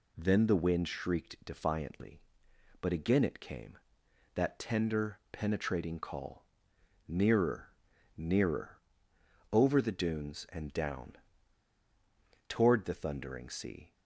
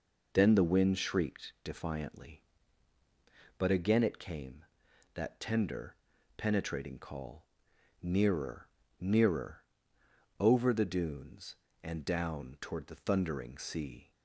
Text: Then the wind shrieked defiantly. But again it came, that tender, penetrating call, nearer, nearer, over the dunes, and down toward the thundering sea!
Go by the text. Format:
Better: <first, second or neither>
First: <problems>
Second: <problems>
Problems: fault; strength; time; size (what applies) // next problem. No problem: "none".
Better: second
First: pauses between "down" and "toward"; strong; at 11.1 s; 1.3 s long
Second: none